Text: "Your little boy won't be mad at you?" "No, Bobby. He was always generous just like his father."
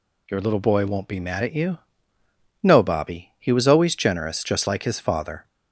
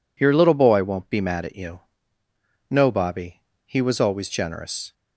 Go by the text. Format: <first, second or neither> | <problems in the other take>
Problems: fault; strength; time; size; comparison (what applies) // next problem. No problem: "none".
first | stops before "just like his father"; at 4.9 s